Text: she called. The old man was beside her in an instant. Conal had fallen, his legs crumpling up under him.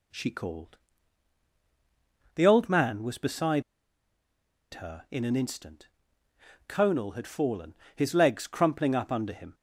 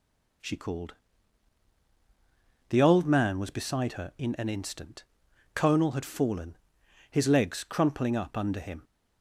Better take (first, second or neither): second